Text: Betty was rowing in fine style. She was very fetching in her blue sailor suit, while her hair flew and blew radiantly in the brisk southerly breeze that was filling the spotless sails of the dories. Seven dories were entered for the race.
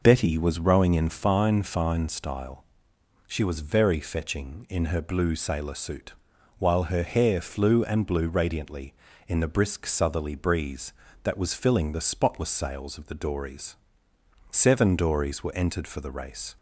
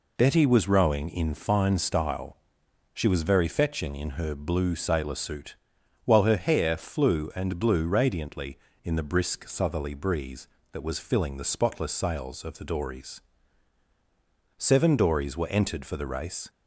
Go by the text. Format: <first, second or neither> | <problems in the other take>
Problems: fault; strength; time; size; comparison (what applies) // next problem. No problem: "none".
second | says "fine" twice; at 1.6 s